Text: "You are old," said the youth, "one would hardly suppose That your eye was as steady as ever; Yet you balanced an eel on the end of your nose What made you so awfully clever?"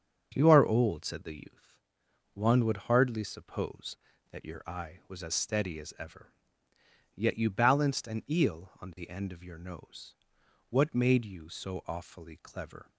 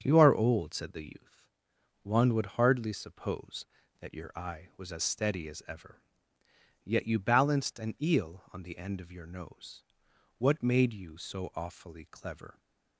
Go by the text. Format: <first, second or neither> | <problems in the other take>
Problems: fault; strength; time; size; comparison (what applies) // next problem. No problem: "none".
neither | starts louder than the rest; the same in both // pauses between "nose" and "What"; noticeable; the same in both